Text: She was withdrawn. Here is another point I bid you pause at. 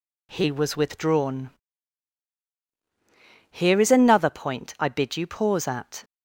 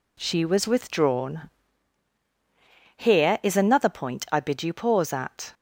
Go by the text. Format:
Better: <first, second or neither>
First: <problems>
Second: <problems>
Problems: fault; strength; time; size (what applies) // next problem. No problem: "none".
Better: second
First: says "He" for "She"; at 0.3 s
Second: none